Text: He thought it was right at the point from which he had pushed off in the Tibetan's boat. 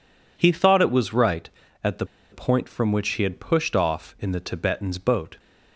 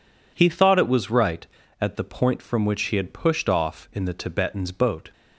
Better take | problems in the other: second | pauses between "the" and "point"; slight; at 2.0 s; 0.27 s long

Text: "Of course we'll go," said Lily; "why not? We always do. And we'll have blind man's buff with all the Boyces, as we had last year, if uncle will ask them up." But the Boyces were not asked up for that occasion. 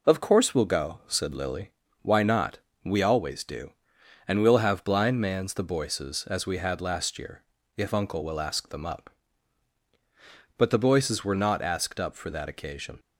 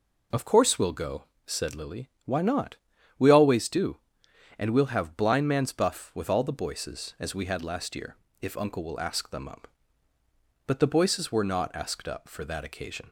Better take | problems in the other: second | skips "buff with all"; at 5.5 s

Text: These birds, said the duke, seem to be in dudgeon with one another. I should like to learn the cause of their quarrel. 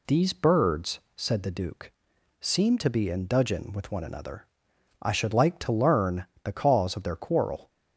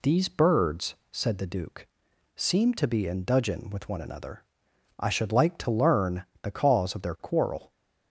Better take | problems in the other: neither | pauses between "learn" and "the"; slight; the same in both

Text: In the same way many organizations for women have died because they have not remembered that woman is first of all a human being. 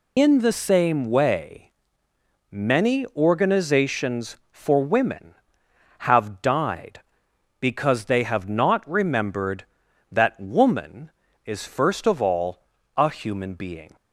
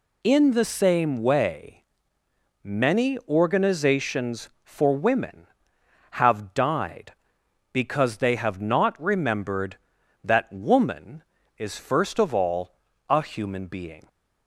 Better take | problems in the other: second | loses the start of "In"; at 0.1 s; 55 ms // pauses between "way" and "many"; noticeable; at 1.7 s; 0.78 s long; noticeable in the second // pauses between "all" and "a"; slight; at 12.6 s; 0.34 s long; slight in the second

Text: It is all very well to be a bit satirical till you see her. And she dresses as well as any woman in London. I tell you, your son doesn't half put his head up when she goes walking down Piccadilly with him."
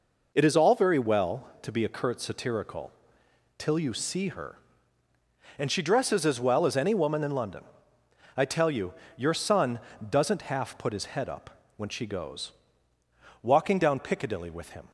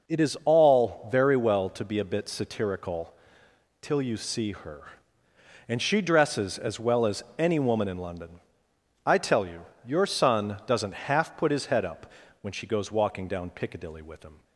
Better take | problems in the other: second | says "curt" for "bit"; at 1.8 s // pauses between "satirical" and "till"; noticeable; at 2.9 s; 0.68 s long; noticeable in the second // pauses between "son" and "doesn't"; slight; at 9.7 s; 0.30 s long // pauses between "up" and "when"; slight; at 11.5 s; 0.26 s long; slight in the second // pauses between "goes" and "walking"; noticeable; at 12.5 s; 0.90 s long

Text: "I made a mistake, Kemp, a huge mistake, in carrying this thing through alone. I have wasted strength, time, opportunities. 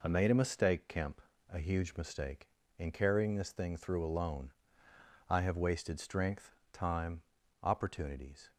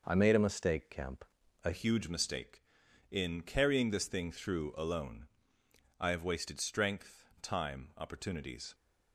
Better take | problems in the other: first | changes voice at "huge"; from 1.7 s on; 7.0 s long

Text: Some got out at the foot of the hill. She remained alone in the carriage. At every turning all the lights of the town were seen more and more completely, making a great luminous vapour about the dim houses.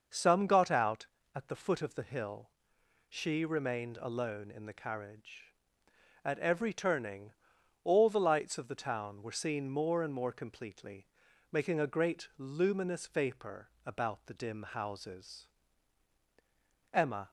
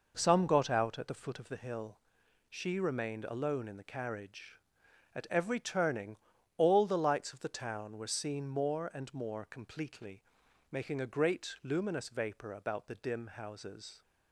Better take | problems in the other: second | starts louder than the rest; noticeable; until 1.4 s; 6 dB // pauses between "turning" and "all"; noticeable; at 7.3 s; 0.50 s long; also in the second // pauses between "vapour" and "about"; slight; at 13.6 s; 0.16 s long // goes on to say "Emma"; slight; from 16.9 s on; 0.38 s long

